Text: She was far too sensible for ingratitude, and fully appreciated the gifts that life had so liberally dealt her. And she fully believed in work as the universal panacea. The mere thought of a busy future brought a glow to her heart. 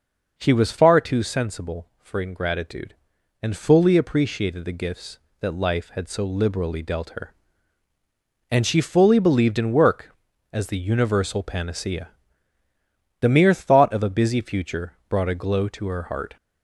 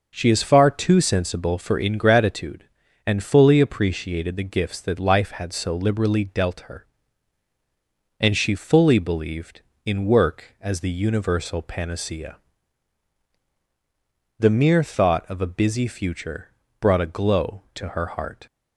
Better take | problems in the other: first | says "is" for "was"; at 0.2 s // pauses between "future" and "brought"; slight; at 16.4 s; 0.30 s long; slight in the first

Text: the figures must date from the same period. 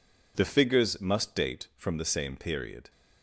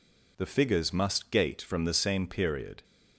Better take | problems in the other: first | says "gate" for "date"; at 1.2 s

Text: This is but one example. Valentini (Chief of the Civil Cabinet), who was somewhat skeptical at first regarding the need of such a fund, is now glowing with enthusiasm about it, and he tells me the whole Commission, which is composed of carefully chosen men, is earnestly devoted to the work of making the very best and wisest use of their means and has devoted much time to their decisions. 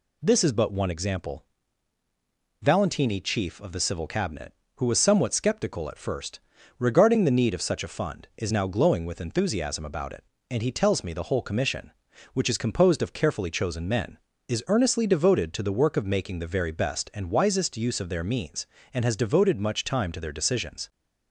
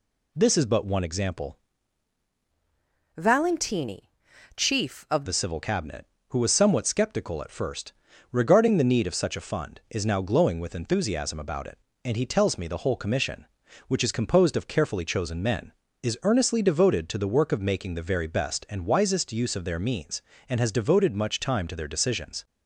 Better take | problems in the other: first | changes voice from "Valentini" to "of"; from 3.1 to 5.2 s; 2.1 s long // pauses between "first" and "regarding"; at 7.9 s; 0.40 s long; also in the first

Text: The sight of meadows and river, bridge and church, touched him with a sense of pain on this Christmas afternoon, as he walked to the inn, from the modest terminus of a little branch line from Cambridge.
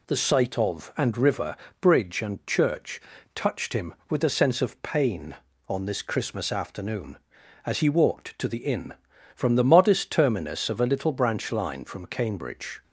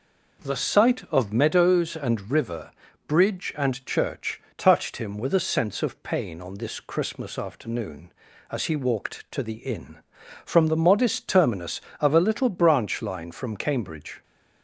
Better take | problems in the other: second | skips "meadows"; at 0.9 s

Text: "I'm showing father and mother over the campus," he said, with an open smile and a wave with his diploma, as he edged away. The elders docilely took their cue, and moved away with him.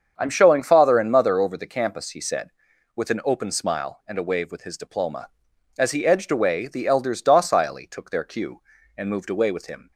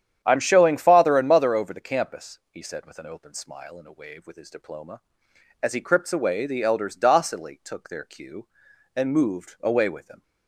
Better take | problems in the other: first | starts louder than the rest; strong; until 1.2 s; 9.5 dB; strong in the first // says "crypts" for "edged"; at 5.8 s

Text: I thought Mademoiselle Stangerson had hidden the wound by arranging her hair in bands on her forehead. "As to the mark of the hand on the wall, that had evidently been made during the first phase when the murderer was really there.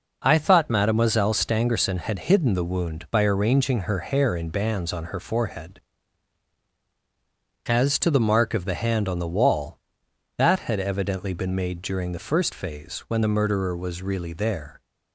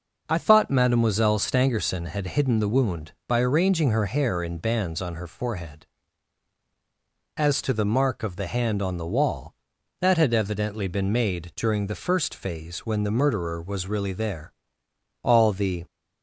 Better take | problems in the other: first | goes on to say "All the"; noticeable; from 15.2 s on; 0.62 s long

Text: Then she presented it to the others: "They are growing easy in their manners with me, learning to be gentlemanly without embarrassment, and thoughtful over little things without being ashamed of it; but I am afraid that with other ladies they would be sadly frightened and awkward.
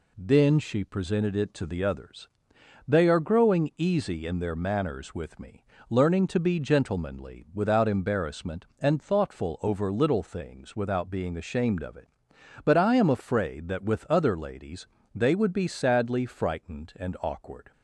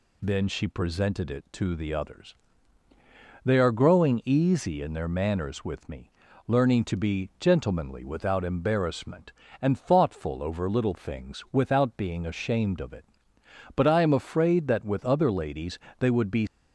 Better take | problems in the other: first | pauses between "ladies" and "they"; slight; at 15.7 s; 0.22 s long; slight in the first // stops before "sadly frightened and awkward"; at 16.4 s

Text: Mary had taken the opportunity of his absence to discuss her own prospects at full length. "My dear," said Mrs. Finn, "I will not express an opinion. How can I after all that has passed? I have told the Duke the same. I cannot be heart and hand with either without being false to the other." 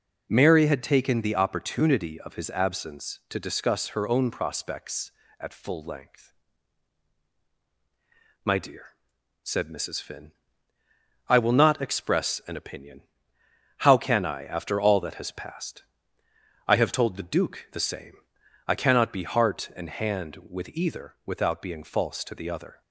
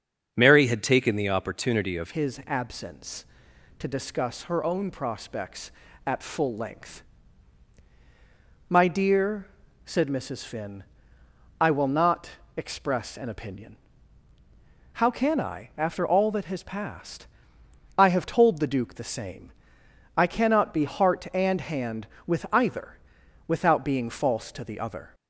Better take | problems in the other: first | starts louder than the rest; until 1.3 s; 7 dB // changes voice at "his"; from 2.1 s on; 23.0 s long // pauses between "not" and "express"; slight; at 12.3 s; 0.26 s long // pauses between "either" and "without"; noticeable; at 22.9 s; 0.50 s long

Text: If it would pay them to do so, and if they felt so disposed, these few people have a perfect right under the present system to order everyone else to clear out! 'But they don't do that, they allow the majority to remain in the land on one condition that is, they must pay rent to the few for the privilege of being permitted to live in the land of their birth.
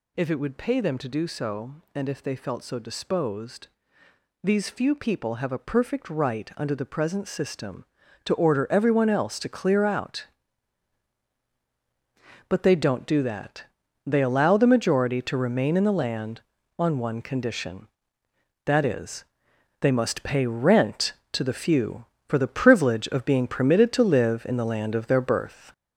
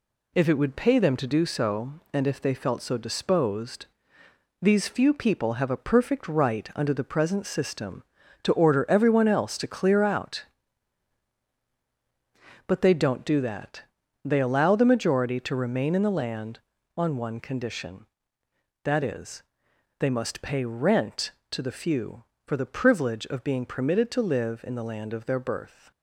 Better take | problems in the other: second | gets louder; noticeable; throughout; 5 dB

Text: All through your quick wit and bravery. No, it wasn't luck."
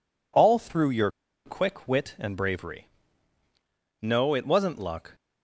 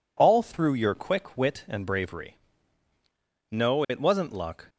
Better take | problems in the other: second | pauses between "your" and "quick"; slight; at 1.1 s; 0.35 s long

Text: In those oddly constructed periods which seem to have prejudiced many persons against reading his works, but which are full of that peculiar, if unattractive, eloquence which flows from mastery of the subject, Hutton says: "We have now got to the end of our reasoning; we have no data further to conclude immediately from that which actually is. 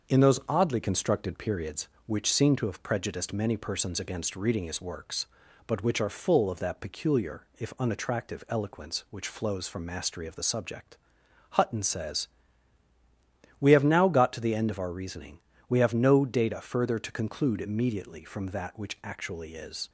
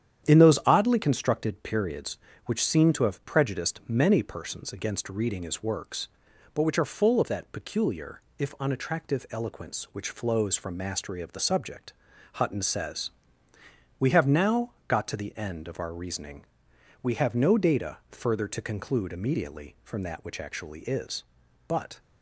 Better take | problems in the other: first | starts louder than the rest; strong; until 1.3 s; 9.5 dB; also in the first // pauses between "now" and "got"; slight; at 14.7 s; 0.16 s long // goes on to say "But"; slight; from 21.6 s on; 0.32 s long

